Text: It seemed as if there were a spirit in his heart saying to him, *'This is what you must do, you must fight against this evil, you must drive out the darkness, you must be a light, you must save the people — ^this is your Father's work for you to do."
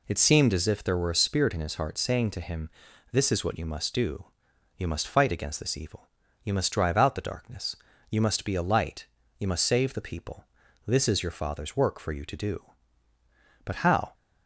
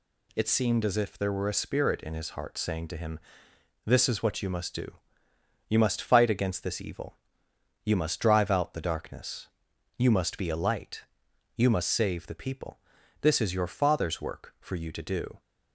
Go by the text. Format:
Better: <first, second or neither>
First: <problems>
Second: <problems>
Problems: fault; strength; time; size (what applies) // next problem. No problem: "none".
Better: second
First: goes on to say "But how"; from 13.6 s on; 0.50 s long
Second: none